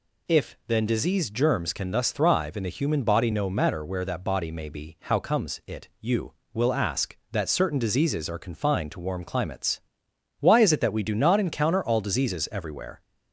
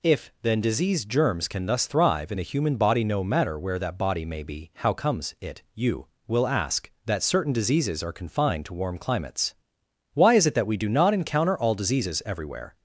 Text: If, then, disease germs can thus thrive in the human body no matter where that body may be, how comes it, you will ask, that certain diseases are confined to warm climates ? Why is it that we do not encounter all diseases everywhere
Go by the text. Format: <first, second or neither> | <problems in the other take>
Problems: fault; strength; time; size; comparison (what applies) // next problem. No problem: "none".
neither | none